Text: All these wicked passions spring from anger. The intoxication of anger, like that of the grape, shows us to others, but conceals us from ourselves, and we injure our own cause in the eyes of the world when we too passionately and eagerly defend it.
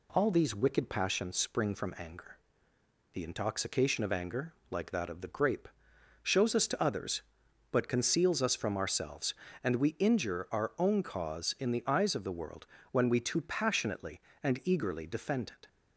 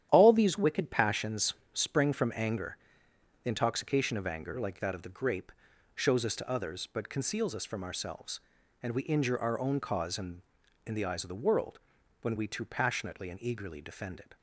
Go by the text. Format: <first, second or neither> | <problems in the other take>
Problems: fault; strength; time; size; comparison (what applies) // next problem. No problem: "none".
first | starts louder than the rest; strong; until 1.1 s; 10.5 dB // pauses between "passions" and "spring"; slight; at 1.5 s; 0.22 s long // says "in" twice; at 10.8 s // pauses between "world" and "when"; at 11.7 s; 0.42 s long; slight in the first